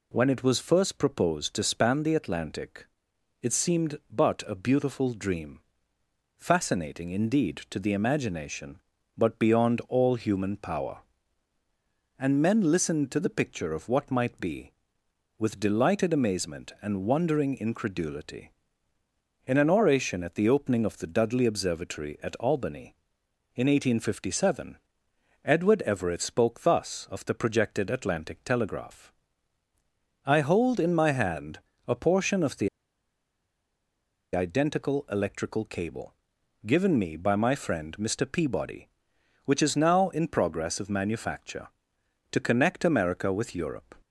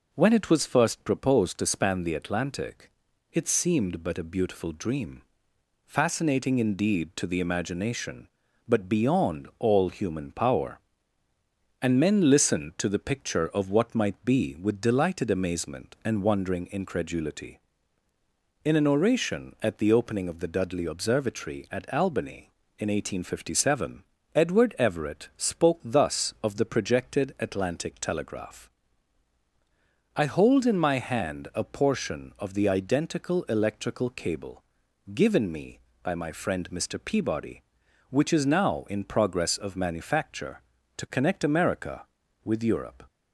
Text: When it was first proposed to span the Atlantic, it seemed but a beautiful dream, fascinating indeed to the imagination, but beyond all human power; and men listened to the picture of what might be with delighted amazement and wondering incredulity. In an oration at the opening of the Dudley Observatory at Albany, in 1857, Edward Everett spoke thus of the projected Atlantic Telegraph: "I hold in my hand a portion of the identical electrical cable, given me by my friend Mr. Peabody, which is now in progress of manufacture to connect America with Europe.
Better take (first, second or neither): second